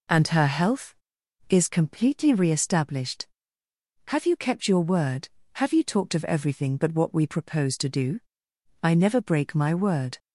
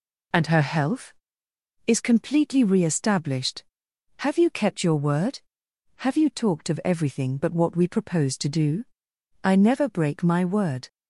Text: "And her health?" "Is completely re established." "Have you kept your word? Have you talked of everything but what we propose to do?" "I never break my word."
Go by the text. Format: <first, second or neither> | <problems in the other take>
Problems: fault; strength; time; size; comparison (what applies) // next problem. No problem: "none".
neither | none